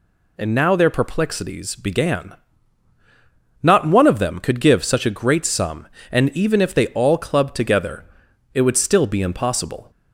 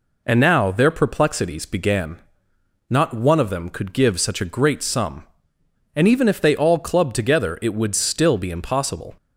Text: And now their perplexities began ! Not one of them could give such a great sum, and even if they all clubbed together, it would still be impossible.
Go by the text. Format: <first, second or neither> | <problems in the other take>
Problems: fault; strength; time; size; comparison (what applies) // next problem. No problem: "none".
neither | none